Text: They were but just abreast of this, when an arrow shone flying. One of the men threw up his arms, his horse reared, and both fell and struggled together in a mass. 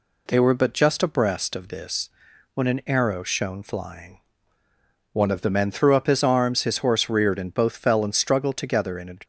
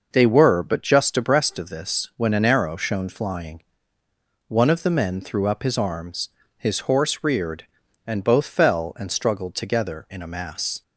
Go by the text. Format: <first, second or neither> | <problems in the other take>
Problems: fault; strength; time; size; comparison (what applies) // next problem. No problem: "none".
second | stops before "mass"; at 9.2 s